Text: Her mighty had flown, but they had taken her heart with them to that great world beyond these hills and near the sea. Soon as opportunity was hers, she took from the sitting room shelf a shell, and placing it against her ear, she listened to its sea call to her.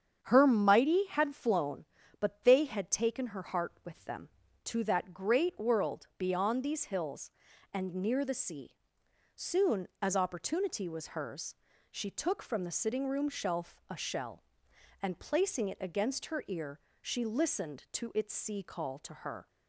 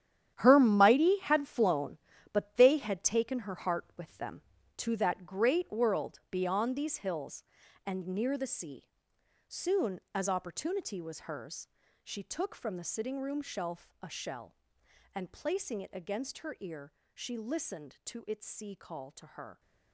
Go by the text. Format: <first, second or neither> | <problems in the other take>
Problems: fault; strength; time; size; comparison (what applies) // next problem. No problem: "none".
first | gets quieter; strong; throughout; 12.5 dB // starts louder than the rest; strong; until 1.3 s; 10 dB; strong in the first